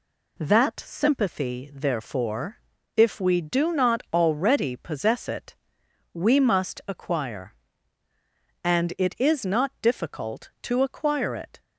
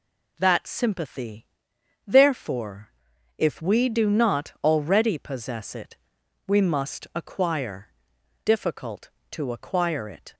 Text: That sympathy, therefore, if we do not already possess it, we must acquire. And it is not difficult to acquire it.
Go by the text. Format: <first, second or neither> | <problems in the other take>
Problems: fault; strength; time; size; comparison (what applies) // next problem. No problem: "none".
first | skips "And it is not"; at 8.1 s